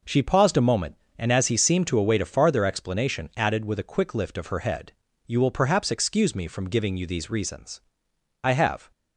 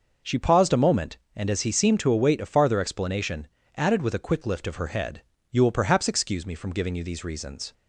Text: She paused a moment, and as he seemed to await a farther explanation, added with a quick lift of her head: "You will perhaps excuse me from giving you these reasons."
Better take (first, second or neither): second